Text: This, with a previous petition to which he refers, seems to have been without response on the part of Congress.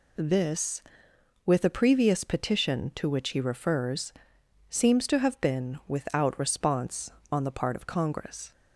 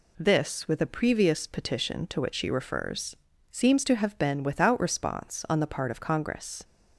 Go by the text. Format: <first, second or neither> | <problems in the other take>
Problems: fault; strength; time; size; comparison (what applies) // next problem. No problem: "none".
first | says "she" for "he"; at 2.3 s